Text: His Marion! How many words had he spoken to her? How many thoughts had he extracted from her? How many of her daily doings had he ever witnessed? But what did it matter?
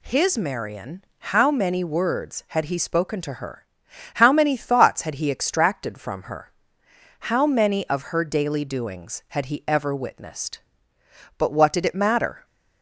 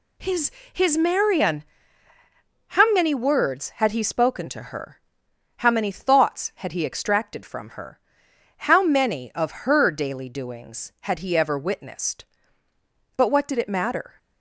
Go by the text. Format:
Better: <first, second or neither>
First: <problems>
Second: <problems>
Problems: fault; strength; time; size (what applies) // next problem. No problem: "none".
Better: first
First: none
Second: says "His" twice; at 0.7 s